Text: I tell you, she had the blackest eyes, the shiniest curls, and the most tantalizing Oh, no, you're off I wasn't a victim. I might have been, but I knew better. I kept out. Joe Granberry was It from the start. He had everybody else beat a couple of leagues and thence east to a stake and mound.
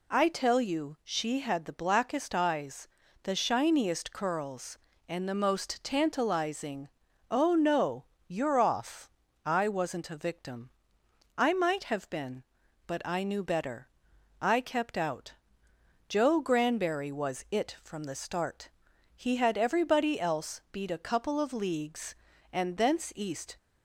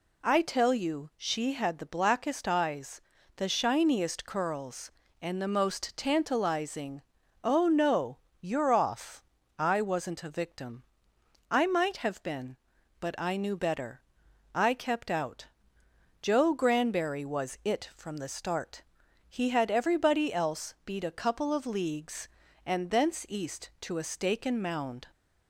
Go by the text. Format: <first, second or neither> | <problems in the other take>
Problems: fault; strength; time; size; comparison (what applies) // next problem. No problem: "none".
second | pauses between "tantalizing" and "Oh"; at 6.8 s; 0.42 s long; also in the second // pauses between "off" and "I"; slight; at 9.0 s; 0.36 s long; slight in the second // stops before "to a stake and mound"; at 23.5 s